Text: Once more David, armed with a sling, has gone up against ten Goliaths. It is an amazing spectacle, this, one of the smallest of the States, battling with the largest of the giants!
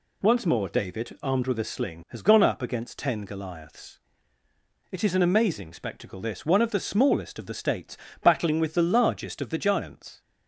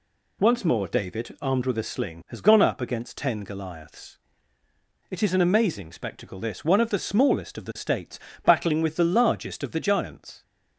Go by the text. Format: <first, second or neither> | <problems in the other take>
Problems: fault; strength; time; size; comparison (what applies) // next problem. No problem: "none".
neither | none